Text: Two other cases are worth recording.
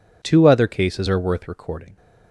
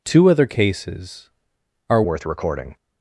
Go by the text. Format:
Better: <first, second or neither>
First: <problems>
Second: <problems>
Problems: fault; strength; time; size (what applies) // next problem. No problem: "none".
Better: first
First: none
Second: changes voice at "worth"; from 2.0 s on; 0.7 s long